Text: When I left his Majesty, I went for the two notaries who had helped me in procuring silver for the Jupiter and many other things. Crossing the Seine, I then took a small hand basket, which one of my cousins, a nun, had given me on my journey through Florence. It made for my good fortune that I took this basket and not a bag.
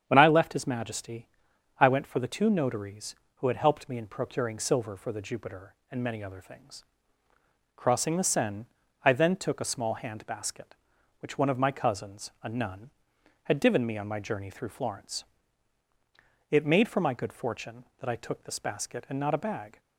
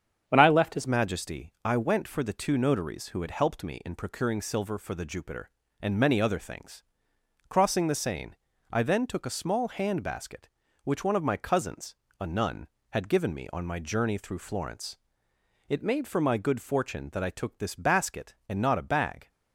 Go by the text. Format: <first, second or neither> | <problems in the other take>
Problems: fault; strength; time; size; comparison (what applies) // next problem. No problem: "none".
first | starts louder than the rest; strong; until 1.2 s; 7.5 dB; strong in the first // changes voice at "Majesty"; from 0.8 s on; 18.4 s long